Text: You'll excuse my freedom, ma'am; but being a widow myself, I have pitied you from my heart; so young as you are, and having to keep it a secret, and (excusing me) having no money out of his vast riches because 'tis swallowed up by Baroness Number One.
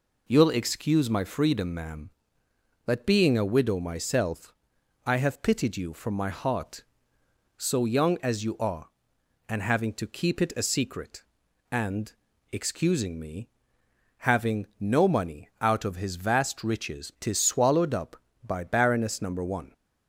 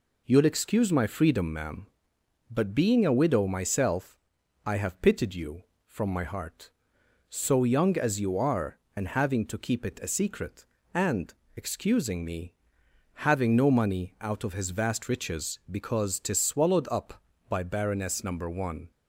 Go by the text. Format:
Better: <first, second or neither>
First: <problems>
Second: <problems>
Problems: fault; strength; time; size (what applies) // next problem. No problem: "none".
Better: second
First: skips "because"; at 17.1 s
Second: none